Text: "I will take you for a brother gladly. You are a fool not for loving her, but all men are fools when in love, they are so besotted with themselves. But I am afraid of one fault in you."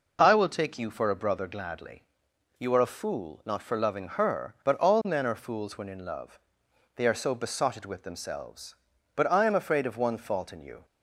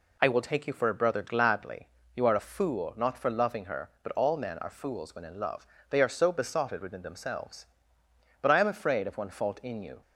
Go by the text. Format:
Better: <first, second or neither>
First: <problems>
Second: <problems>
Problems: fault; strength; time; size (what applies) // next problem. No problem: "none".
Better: first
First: none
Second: says "within" for "with"; at 6.8 s